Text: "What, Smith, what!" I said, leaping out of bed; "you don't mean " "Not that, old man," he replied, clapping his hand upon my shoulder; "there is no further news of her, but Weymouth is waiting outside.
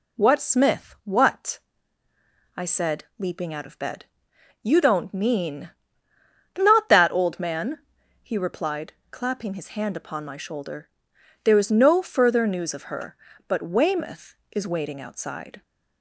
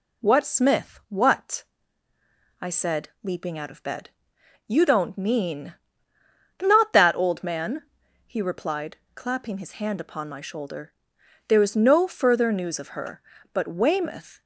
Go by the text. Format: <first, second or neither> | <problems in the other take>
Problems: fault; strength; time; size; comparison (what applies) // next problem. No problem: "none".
first | stops before "is waiting outside"; at 14.4 s